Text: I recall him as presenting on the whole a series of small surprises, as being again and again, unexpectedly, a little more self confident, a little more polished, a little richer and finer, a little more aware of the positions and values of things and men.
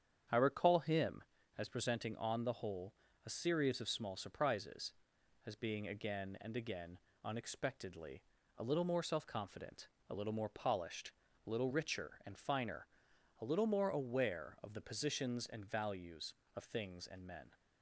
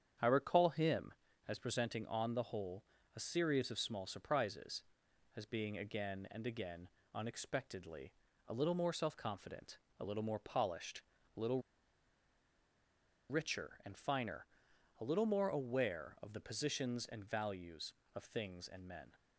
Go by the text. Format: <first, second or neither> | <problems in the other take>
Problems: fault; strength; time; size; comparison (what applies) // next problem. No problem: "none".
first | starts louder than the rest; strong; until 1.5 s; 8.5 dB; strong in the first // pauses between "whole" and "a"; slight; at 2.8 s; 0.32 s long; slight in the first // pauses between "little" and "richer"; strong; at 11.6 s; 1.6 s long